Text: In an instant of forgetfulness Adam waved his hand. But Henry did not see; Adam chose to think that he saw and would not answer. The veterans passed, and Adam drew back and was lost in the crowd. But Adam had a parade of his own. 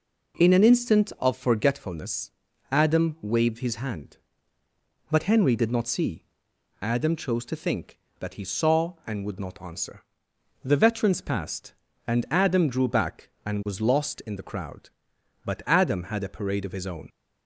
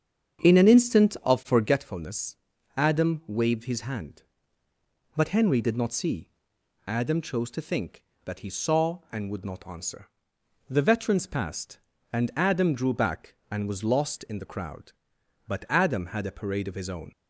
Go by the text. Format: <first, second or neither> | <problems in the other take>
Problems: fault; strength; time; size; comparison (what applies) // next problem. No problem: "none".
first | starts louder than the rest; strong; until 1.8 s; 7.5 dB // pauses between "forgetfulness" and "Adam"; at 2.3 s; 0.40 s long; also in the first